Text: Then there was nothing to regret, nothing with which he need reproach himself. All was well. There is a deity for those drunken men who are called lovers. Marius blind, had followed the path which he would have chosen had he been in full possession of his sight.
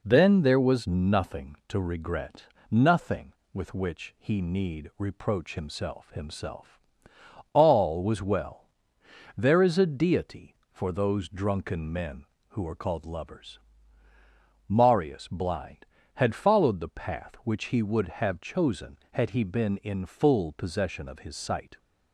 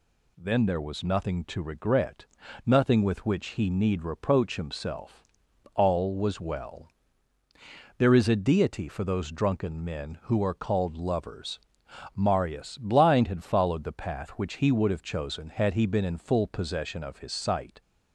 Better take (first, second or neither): second